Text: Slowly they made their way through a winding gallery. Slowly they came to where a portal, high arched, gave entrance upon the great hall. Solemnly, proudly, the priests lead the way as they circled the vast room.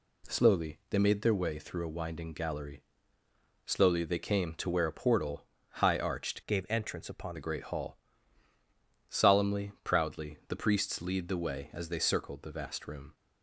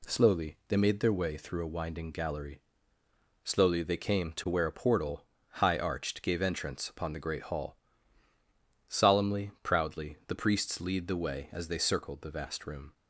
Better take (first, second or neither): second